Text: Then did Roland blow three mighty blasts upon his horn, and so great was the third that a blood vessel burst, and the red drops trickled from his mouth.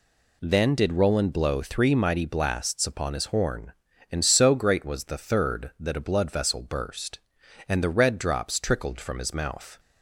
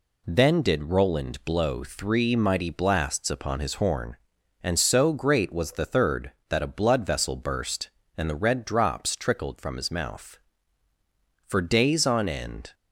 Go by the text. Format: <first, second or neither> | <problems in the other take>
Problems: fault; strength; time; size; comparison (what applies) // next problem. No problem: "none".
first | goes on to say "For days on end"; noticeable; from 11.4 s on; 1.2 s long